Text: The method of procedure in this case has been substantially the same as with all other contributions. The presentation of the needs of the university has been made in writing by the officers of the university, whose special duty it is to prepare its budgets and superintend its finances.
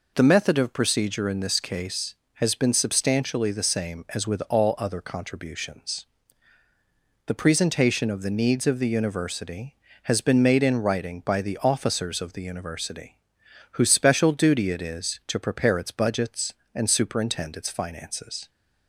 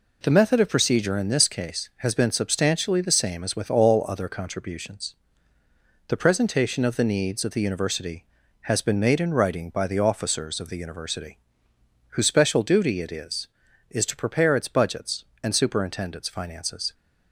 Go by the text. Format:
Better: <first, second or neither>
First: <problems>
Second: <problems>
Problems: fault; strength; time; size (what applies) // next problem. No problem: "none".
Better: first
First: none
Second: says "is" twice; at 13.8 s